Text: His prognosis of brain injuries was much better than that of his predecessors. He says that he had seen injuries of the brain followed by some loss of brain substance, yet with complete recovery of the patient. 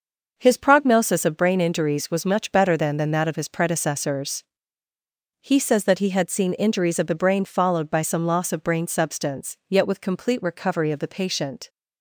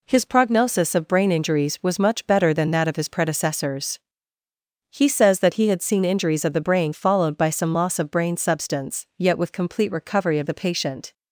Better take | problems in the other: second | starts louder than the rest; noticeable; until 1.3 s; 6 dB // says "than" twice; at 2.9 s

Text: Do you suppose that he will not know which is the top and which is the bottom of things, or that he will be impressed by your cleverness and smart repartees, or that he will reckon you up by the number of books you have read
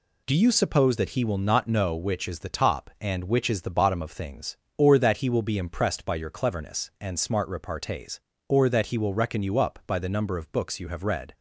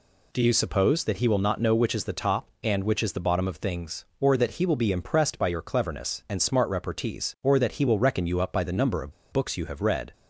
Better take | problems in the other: first | pauses between "of" and "books"; slight; at 9.1 s; 0.19 s long

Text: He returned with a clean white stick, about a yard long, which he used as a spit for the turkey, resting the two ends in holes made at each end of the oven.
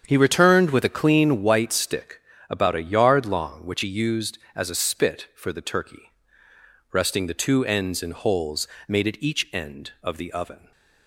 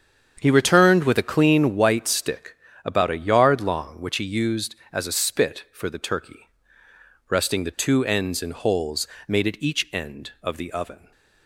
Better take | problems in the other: neither | starts louder than the rest; strong; the same in both // pauses between "holes" and "made"; slight; the same in both

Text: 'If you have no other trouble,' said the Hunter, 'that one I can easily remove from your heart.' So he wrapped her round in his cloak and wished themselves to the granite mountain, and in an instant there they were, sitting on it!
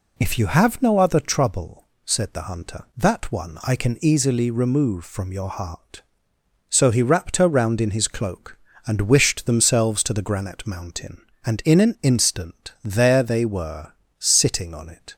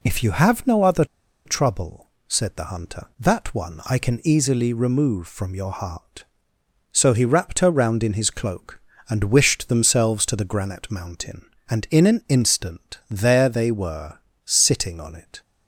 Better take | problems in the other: first | pauses between "other" and "trouble"; at 1.0 s; 0.40 s long

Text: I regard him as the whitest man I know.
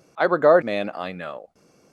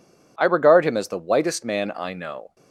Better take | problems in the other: second | skips "him as the whitest"; at 0.6 s

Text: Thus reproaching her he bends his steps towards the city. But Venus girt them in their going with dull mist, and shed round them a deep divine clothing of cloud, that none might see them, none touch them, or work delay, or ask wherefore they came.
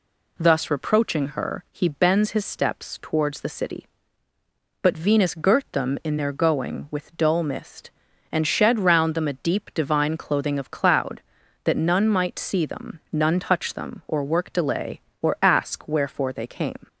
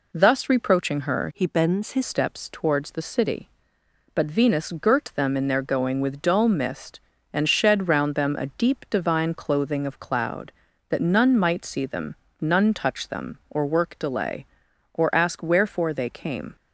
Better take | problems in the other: first | changes voice from "he" to "his"; from 1.3 to 2.0 s; 0.7 s long

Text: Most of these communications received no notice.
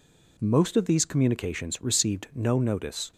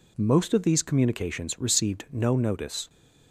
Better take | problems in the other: neither | none

